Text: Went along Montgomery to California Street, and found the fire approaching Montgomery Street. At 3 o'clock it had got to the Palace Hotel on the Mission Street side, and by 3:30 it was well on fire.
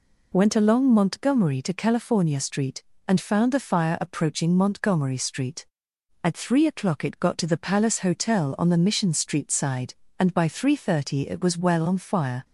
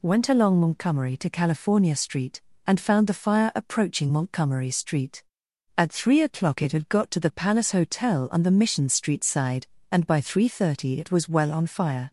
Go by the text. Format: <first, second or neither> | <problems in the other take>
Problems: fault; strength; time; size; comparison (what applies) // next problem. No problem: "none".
second | skips "had"; at 7.1 s